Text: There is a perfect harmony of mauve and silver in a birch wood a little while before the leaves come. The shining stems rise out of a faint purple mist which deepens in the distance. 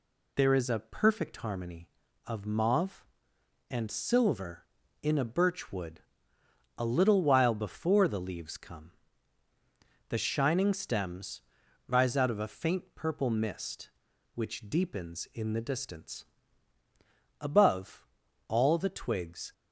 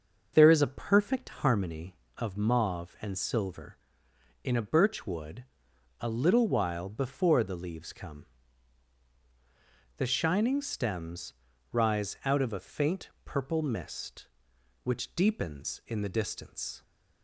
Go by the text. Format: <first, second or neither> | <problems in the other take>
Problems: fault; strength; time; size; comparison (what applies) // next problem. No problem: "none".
second | pauses between "wood" and "a"; noticeable; at 6.0 s; 0.78 s long; noticeable in the second // pauses between "stems" and "rise"; noticeable; at 11.4 s; 0.46 s long; slight in the second // goes on to say "Above all the twigs"; strong; from 17.4 s on; 2.1 s long